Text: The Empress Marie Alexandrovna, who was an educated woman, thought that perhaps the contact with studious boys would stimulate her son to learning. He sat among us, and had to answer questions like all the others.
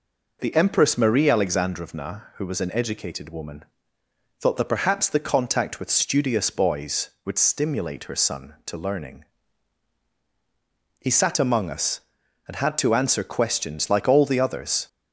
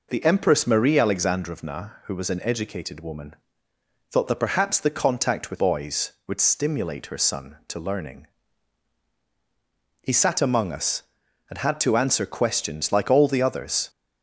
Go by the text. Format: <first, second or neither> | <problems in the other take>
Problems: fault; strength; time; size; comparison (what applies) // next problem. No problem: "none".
first | skips "studious"; at 5.5 s